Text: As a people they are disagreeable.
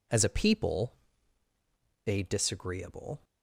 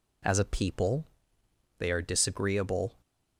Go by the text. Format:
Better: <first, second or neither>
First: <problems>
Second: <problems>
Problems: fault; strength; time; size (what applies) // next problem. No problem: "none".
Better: second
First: pauses between "people" and "they"; at 0.9 s; 1.1 s long // skips "are"; at 2.2 s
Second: pauses between "people" and "they"; noticeable; at 1.0 s; 0.74 s long